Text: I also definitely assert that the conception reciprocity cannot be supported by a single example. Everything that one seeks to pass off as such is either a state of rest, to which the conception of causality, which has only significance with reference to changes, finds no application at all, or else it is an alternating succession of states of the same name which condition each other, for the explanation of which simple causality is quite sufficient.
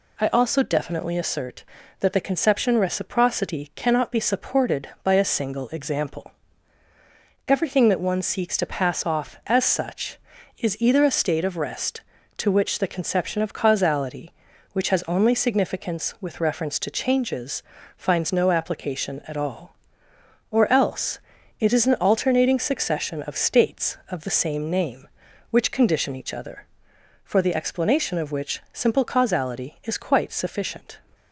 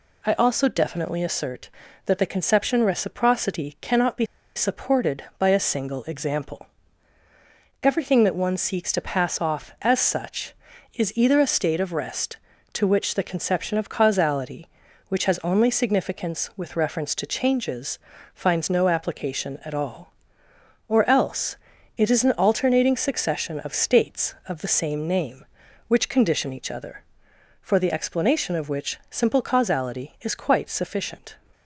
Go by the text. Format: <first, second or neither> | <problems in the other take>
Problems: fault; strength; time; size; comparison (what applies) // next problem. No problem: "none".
first | pauses between "be" and "supported"; slight; at 4.2 s; 0.29 s long // pauses between "else" and "it"; at 21.5 s; 0.38 s long; also in the first